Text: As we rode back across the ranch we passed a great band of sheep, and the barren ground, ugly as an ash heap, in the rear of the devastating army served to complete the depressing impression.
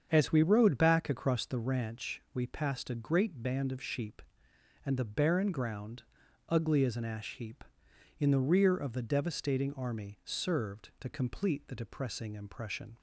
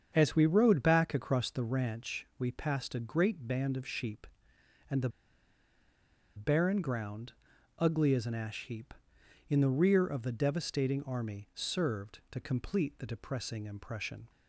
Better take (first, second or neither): first